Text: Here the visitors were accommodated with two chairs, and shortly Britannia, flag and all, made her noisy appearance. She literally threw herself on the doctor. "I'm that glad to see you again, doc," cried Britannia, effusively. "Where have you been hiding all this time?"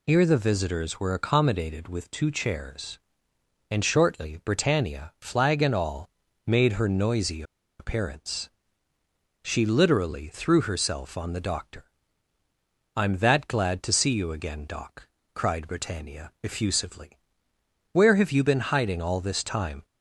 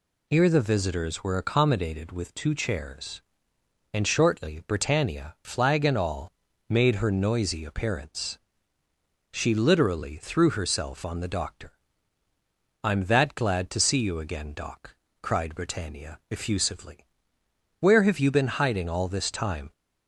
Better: second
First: pauses between "noisy" and "appearance"; at 7.4 s; 0.36 s long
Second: none

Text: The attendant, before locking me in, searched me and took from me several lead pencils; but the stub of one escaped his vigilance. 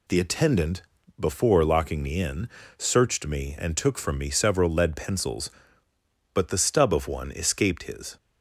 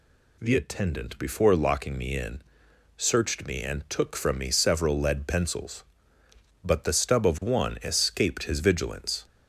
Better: second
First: stops before "vigilance"; at 8.1 s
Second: none

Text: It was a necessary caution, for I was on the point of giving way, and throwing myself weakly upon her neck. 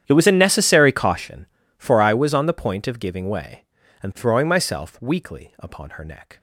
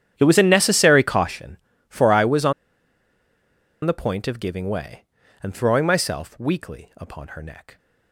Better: first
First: starts louder than the rest; strong; until 1.0 s; 10 dB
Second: starts louder than the rest; strong; until 1.1 s; 10 dB // pauses between "on" and "the"; strong; at 2.5 s; 1.3 s long

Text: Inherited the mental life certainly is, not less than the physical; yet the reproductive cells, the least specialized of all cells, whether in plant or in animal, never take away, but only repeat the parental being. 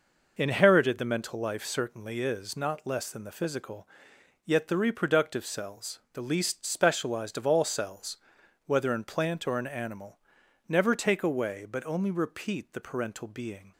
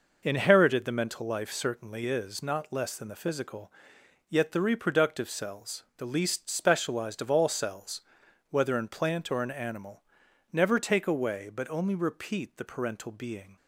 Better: neither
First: none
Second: none

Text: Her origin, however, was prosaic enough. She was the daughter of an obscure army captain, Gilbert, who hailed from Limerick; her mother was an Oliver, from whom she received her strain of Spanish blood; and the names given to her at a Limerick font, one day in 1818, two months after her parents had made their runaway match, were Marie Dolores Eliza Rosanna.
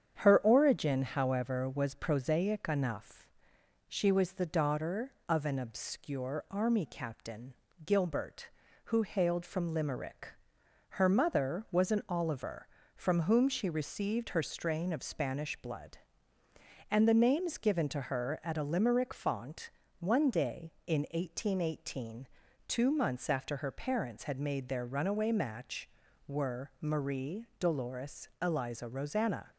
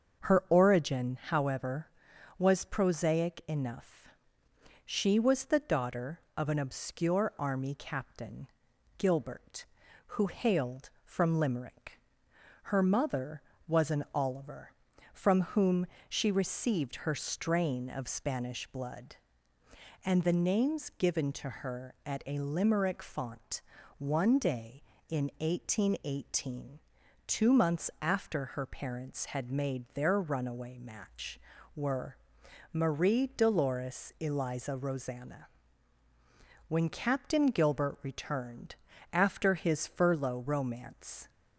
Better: first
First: starts louder than the rest; strong; until 1.2 s; 8 dB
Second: starts louder than the rest; until 1.4 s; 7 dB // pauses between "whom" and "she"; slight; at 15.8 s; 0.22 s long // pauses between "were" and "Marie"; noticeable; at 32.1 s; 0.56 s long // goes on to say "When Captain Gilbert returned after his furlough romance"; strong; from 36.6 s on; 4.6 s long

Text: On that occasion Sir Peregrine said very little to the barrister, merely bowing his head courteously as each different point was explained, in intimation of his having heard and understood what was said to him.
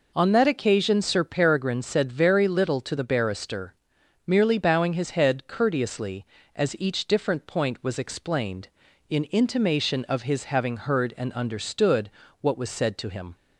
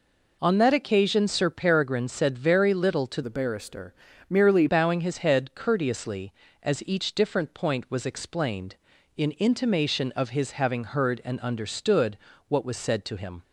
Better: first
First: pauses between "understood" and "what"; slight; at 12.0 s; 0.30 s long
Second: changes voice from "the" to "merely"; from 3.2 to 4.6 s; 1.4 s long // pauses between "understood" and "what"; slight; at 12.1 s; 0.30 s long

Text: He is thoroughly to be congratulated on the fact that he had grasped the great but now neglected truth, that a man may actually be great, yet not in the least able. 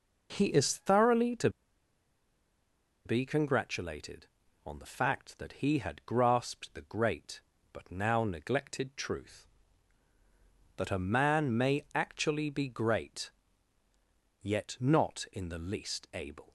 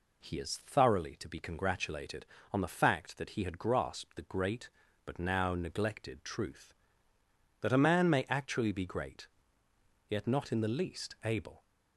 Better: second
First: pauses between "to" and "be"; strong; at 1.4 s; 1.5 s long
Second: none

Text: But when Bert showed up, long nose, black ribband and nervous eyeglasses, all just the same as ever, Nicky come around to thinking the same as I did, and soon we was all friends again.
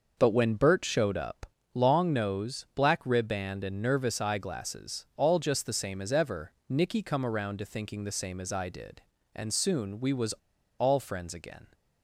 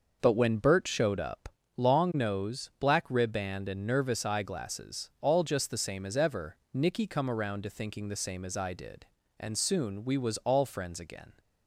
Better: second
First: starts louder than the rest; noticeable; until 1.2 s; 6 dB // pauses between "was" and "all"; at 10.3 s; 0.45 s long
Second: starts louder than the rest; noticeable; until 1.2 s; 6 dB

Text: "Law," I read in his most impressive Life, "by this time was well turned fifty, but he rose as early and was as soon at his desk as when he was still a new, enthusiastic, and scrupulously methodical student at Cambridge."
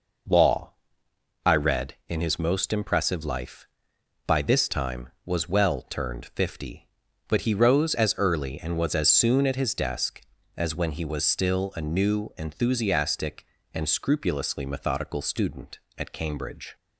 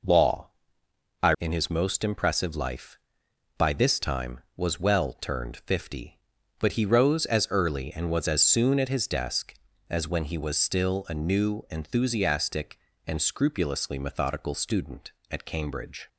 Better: first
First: none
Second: skips "read"; at 1.3 s

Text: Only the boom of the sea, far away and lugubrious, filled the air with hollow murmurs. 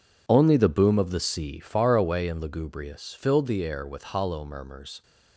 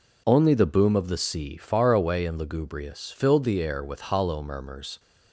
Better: second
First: gets quieter; strong; throughout; 13 dB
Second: none

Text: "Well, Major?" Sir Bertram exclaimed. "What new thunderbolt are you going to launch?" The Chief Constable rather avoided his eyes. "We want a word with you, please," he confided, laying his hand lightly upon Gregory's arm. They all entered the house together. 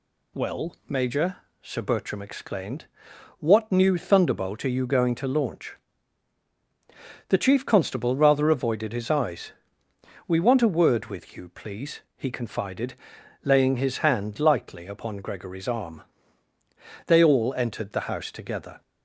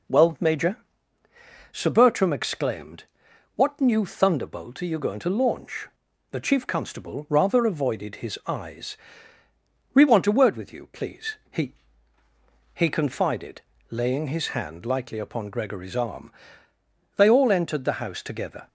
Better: first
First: none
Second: says "he" twice; at 12.7 s

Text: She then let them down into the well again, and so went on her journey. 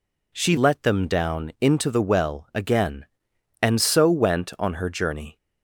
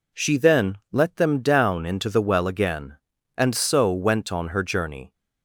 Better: second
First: skips "then"; at 0.5 s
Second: none

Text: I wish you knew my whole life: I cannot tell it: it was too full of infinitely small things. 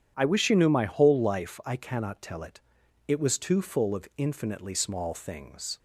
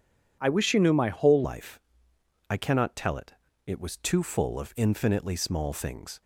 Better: first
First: none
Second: changes voice at "life"; from 1.4 s on; 4.8 s long

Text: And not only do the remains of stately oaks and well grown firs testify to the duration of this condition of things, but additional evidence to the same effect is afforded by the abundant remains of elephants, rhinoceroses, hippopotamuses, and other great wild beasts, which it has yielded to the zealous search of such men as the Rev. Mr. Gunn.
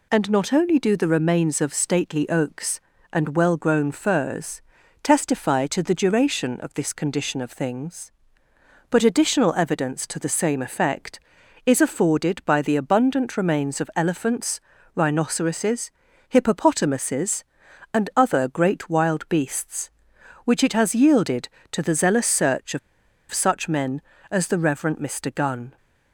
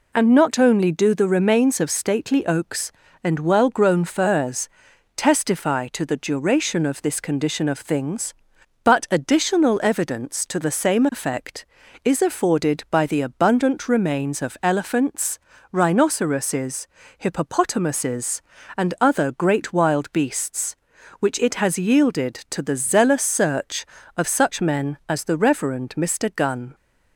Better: second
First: pauses between "firs" and "testify"; at 4.6 s; 0.40 s long // pauses between "of" and "such"; noticeable; at 22.7 s; 0.52 s long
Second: pauses between "firs" and "testify"; noticeable; at 4.6 s; 0.48 s long

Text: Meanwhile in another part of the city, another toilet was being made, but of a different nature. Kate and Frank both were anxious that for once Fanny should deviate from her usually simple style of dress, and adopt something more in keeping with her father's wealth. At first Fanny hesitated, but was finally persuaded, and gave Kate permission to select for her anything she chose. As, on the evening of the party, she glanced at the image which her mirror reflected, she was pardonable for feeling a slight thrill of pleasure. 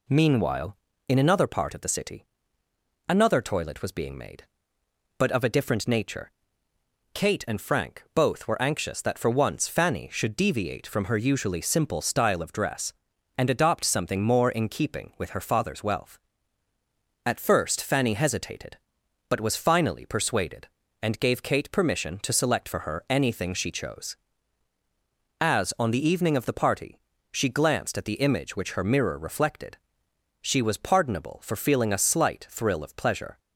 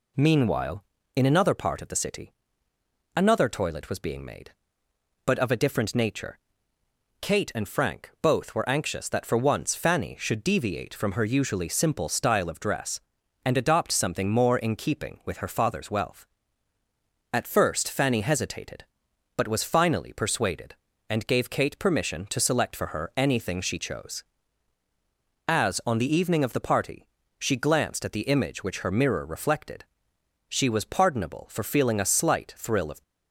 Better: first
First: none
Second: stops before "pleasure"; at 33.0 s

